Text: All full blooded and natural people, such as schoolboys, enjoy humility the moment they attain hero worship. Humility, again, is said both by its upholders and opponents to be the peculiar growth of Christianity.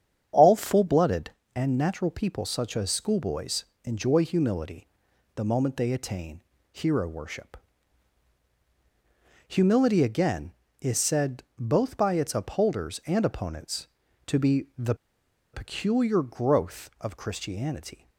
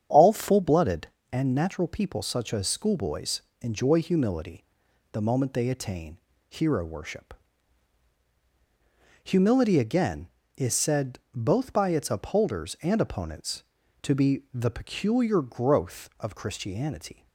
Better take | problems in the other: second | starts louder than the rest; strong; until 1.5 s; 8.5 dB; strong in the second // pauses between "humility" and "the"; noticeable; at 4.8 s; 0.48 s long; noticeable in the second // pauses between "attain" and "hero"; slight; at 6.4 s; 0.32 s long; slight in the second // pauses between "the" and "peculiar"; noticeable; at 14.9 s; 0.59 s long

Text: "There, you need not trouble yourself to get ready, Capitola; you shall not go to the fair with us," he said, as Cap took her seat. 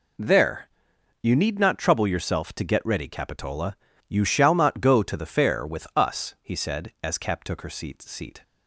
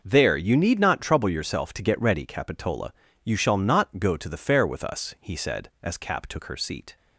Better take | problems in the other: second | says "seat" twice; at 8.0 s

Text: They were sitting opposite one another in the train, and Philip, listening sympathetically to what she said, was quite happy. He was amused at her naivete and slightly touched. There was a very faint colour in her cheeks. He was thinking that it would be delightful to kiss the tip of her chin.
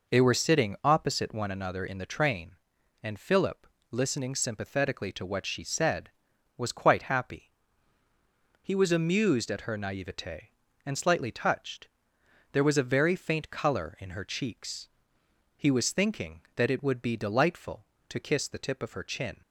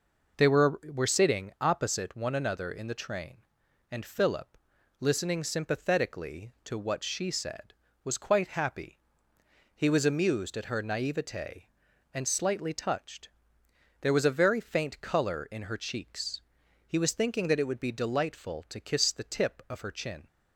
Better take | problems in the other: first | says "were" twice; at 0.8 s

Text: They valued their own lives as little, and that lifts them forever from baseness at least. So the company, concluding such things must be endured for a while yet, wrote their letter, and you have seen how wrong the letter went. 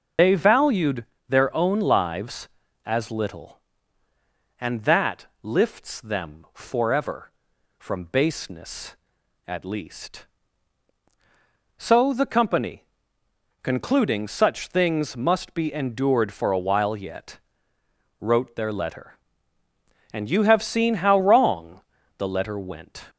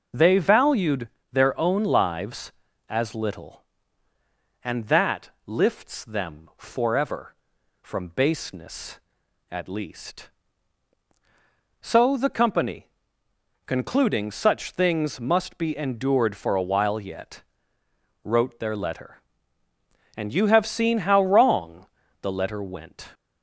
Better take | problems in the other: second | loses the start of "They"; at 0.1 s; 95 ms // pauses between "valued" and "their"; slight; at 1.0 s; 0.24 s long; slight in the second // pauses between "that" and "lifts"; slight; at 5.2 s; 0.18 s long; slight in the second // pauses between "wrong" and "the"; at 21.7 s; 0.38 s long; also in the second

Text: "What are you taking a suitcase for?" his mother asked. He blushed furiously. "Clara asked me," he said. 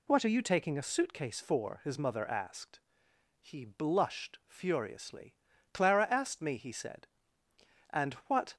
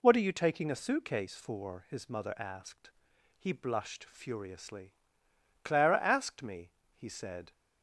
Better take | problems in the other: second | goes on to say "And what"; noticeable; from 7.9 s on; 0.64 s long

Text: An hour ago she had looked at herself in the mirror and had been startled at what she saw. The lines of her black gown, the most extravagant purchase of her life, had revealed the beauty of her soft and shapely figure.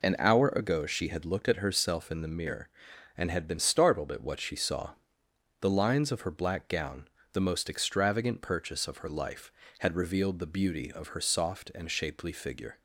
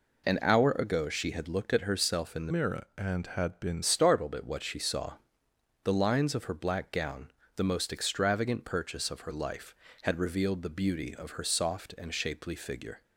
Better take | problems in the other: first | changes voice from "mirror" to "been"; from 2.5 to 3.8 s; 1.3 s long

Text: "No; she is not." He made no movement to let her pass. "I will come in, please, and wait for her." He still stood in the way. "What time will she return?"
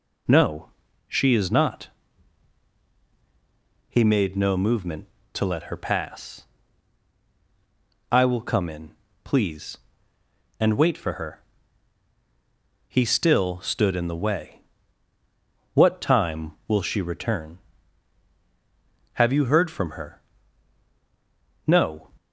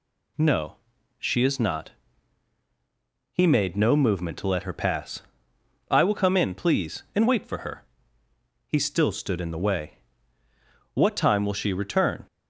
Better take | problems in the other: second | goes on to say "Have you heard from her No"; strong; from 19.1 s on; 2.9 s long

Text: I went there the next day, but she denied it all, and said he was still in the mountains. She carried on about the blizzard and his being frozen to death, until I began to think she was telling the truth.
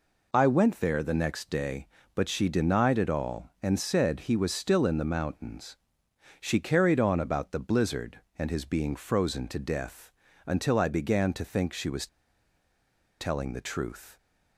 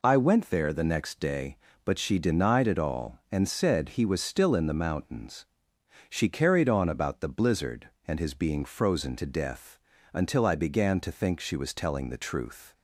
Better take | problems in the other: second | pauses between "was" and "telling"; at 12.0 s; 1.1 s long

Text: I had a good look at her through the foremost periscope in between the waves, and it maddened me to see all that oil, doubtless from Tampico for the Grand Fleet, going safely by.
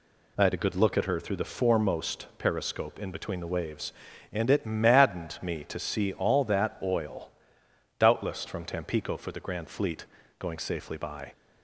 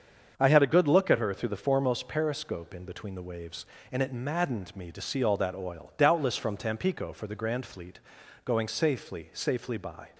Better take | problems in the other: first | starts louder than the rest; until 1.3 s; 7 dB // says "safely" twice; at 9.3 s

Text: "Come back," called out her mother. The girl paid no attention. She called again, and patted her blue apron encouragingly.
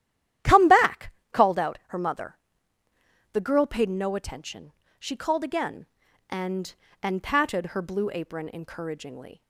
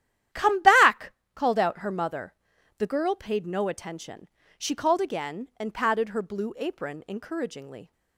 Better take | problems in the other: second | starts louder than the rest; strong; until 1.6 s; 12 dB; strong in the second // says "and" twice; at 7.0 s

